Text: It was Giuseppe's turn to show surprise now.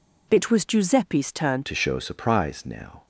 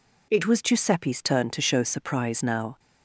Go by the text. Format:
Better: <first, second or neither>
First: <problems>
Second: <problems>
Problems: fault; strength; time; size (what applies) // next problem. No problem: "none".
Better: second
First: changes voice at "to"; from 1.6 s on; 1.4 s long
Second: none